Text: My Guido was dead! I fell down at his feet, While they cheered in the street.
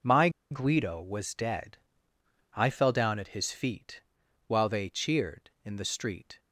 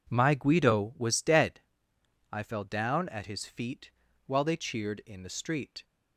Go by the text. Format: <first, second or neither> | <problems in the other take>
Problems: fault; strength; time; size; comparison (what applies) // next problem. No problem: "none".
second | pauses between "My" and "Guido"; slight; at 0.2 s; 0.21 s long